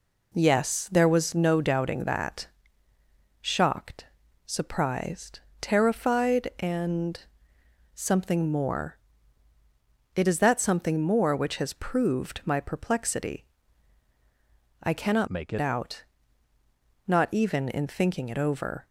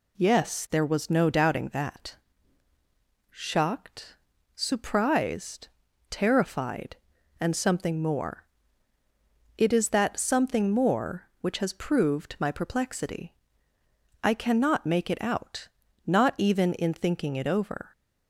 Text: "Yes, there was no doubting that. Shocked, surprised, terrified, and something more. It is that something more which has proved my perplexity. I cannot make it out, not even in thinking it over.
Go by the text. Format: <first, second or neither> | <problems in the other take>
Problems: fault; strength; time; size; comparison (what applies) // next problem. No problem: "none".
second | pauses between "and" and "something"; noticeable; at 7.1 s; 0.74 s long // changes voice from "make" to "it"; from 15.2 to 15.5 s; 0.3 s long